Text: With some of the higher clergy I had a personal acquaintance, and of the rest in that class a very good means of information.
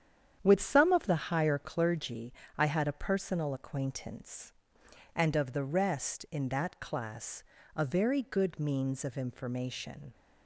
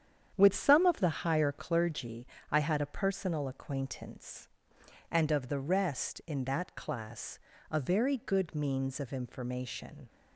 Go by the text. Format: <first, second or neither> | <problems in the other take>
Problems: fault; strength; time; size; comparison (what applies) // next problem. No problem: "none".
neither | starts louder than the rest; strong; the same in both // pauses between "clergy" and "I"; slight; the same in both // pauses between "class" and "a"; slight; the same in both